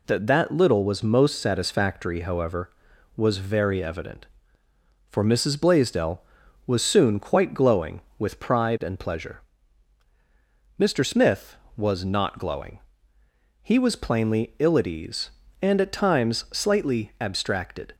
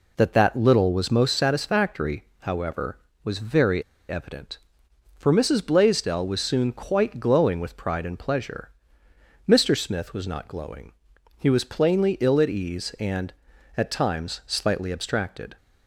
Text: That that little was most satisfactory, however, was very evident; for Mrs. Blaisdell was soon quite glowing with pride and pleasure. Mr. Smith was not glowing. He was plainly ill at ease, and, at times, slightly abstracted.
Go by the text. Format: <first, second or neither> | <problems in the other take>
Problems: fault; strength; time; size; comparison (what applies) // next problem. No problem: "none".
first | pauses between "very" and "evident"; slight; at 3.8 s; 0.26 s long